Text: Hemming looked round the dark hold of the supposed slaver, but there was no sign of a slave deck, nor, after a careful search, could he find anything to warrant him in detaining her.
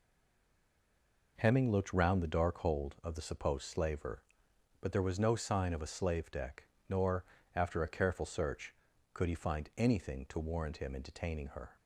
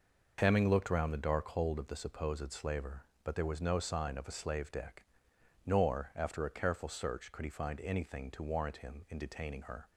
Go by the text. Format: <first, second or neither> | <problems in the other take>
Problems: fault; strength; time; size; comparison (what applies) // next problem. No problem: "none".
second | stays silent before the first word; noticeable; until 1.3 s; 1.3 s long